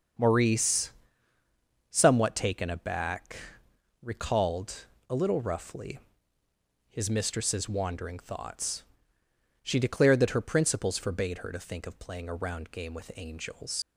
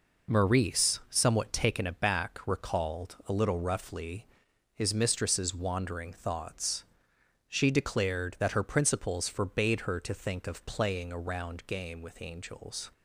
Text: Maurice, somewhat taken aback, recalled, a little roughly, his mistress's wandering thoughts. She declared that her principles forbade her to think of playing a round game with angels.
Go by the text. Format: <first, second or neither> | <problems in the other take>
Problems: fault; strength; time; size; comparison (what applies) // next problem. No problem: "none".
second | starts louder than the rest; until 2.1 s; 6.5 dB // leaves "angels" unfinished; at 13.8 s; 85 ms